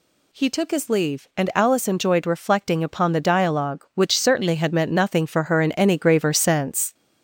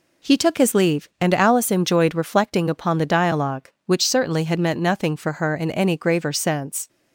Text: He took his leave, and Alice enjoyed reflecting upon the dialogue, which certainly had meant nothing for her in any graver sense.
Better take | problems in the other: second | gets louder; throughout; 3.5 dB

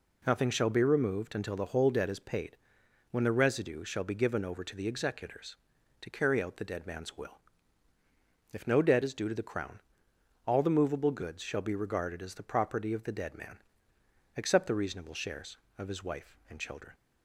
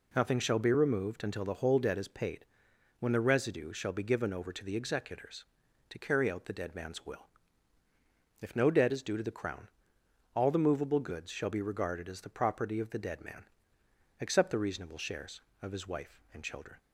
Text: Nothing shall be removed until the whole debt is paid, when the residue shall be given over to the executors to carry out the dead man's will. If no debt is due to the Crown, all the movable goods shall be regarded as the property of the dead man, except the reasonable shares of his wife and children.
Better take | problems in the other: neither | none

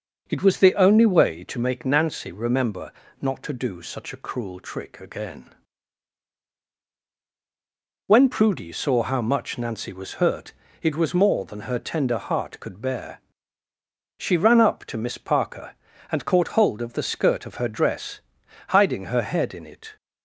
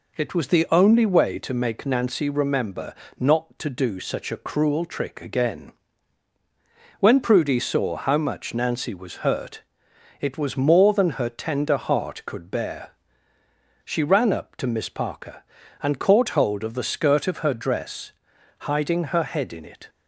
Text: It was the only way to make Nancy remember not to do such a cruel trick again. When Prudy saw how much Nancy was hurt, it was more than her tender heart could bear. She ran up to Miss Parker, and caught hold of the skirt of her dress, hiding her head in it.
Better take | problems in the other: second | starts louder than the rest; noticeable; until 1.5 s; 6 dB // pauses between "remember" and "not"; slight; at 2.9 s; 0.30 s long; slight in the second

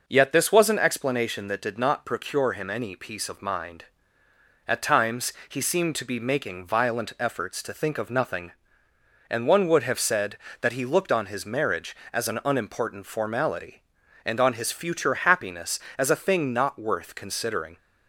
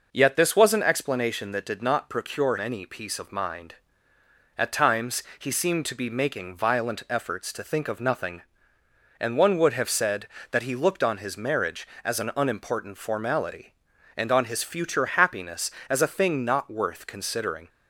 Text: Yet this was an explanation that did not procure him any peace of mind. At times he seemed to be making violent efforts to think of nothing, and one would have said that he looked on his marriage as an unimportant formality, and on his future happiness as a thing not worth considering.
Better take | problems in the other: first | skips "him"; at 2.5 s // pauses between "times" and "he"; slight; at 5.2 s; 0.16 s long; slight in the first

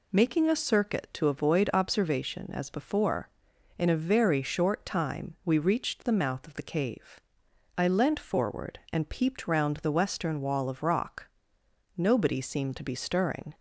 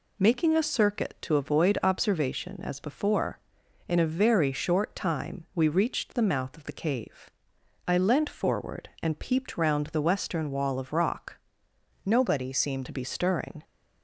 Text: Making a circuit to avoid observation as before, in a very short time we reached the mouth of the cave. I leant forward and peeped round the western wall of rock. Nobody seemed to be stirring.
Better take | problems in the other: first | changes voice from "Nobody" to "seemed"; from 12.0 to 12.8 s; 0.8 s long

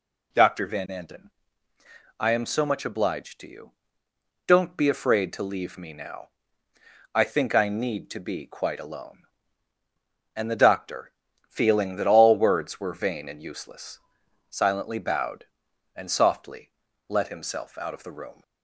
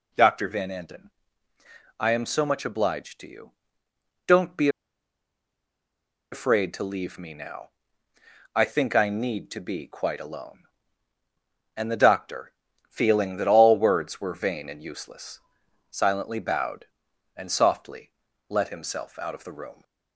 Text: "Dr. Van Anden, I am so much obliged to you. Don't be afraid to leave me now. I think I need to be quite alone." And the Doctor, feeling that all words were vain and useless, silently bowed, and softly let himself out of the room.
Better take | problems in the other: first | pauses between "be" and "afraid"; strong; at 4.6 s; 1.6 s long // pauses between "softly" and "let"; slight; at 18.1 s; 0.36 s long; slight in the first

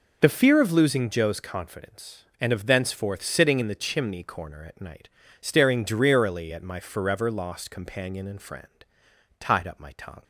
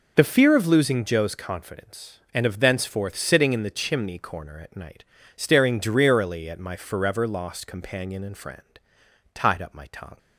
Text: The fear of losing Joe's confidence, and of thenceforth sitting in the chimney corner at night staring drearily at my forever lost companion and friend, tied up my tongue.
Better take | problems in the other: neither | pauses between "night" and "staring"; slight; the same in both

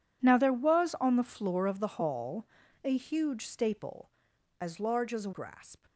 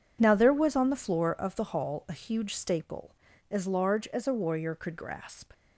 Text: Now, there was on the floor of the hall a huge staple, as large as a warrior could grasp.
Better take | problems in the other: second | pauses between "hall" and "a"; at 2.4 s; 0.40 s long // skips "warrior could"; at 5.3 s

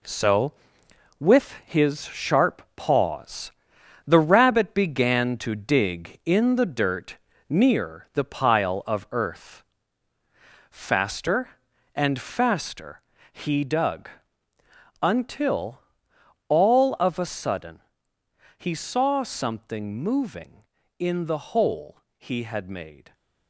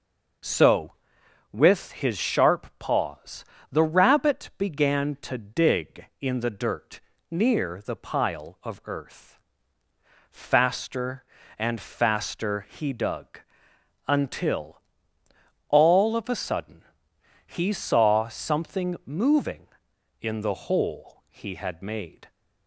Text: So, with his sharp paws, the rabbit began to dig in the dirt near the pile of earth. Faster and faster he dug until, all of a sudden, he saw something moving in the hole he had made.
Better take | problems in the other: second | gets quieter; strong; throughout; 8 dB // pauses between "dirt" and "near"; slight; at 7.1 s; 0.32 s long; slight in the second // pauses between "faster" and "he"; slight; at 13.0 s; 0.30 s long // pauses between "dug" and "until"; noticeable; at 14.0 s; 0.92 s long; noticeable in the second // pauses between "hole" and "he"; slight; at 21.9 s; 0.18 s long

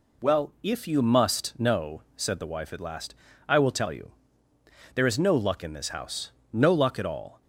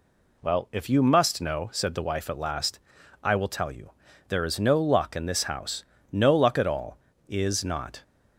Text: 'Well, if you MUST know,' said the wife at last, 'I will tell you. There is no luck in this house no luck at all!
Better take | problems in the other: first | pauses between "house" and "no"; slight; at 5.8 s; 0.30 s long; slight in the first // goes on to say "Is not"; noticeable; from 7.2 s on; 0.76 s long

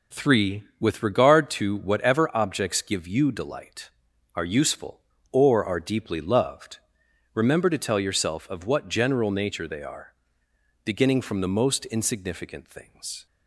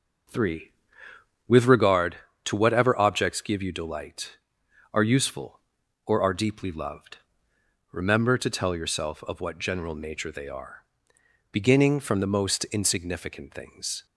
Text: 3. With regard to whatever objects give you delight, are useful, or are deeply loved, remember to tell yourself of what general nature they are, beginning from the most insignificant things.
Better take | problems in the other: first | starts louder than the rest; noticeable; until 1.9 s; 6 dB

